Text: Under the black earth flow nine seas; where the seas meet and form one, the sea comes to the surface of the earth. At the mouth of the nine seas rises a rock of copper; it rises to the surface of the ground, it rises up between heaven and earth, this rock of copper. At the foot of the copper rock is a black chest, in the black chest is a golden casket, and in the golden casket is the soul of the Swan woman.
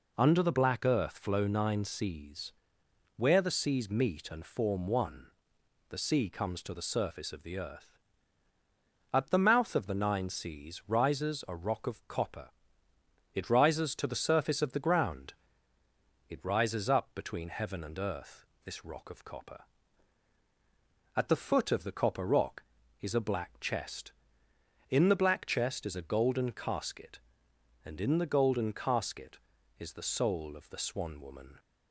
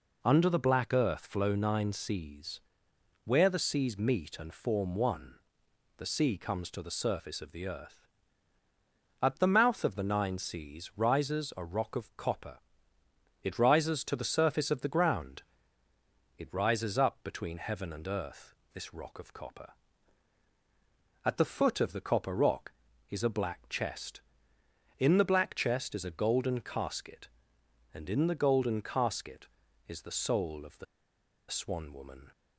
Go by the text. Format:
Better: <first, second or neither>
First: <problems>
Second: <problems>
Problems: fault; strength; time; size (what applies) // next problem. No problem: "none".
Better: first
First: none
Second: pauses between "the" and "Swan"; noticeable; at 30.8 s; 0.65 s long